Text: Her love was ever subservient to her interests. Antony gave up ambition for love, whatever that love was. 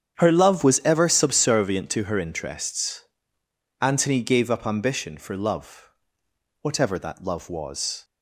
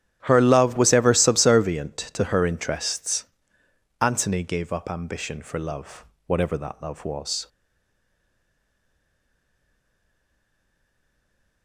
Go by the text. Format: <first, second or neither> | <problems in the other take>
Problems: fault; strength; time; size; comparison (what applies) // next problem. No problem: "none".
first | starts louder than the rest; strong; until 1.2 s; 10.5 dB; strong in the first // stays silent after the last word; strong; from 7.4 s on; 4.2 s long